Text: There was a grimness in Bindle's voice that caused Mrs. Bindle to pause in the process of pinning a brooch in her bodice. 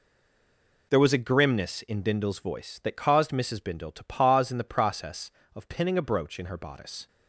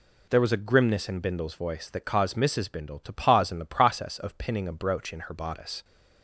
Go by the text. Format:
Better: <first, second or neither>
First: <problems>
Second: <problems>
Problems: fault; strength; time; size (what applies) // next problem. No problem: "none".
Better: second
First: stays silent before the first word; slight; until 0.9 s; 0.9 s long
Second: none